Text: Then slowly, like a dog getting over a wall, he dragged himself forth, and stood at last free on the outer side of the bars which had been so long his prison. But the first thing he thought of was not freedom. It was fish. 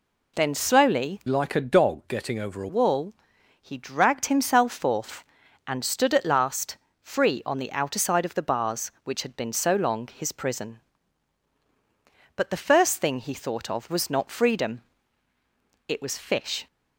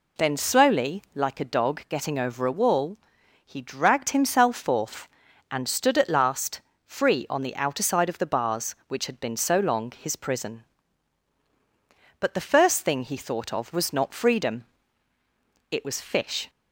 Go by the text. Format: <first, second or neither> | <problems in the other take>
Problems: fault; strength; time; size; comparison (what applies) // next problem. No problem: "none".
second | changes voice from "like" to "a"; from 1.2 to 2.6 s; 1.4 s long // pauses between "last" and "free"; slight; at 6.7 s; 0.24 s long; slight in the second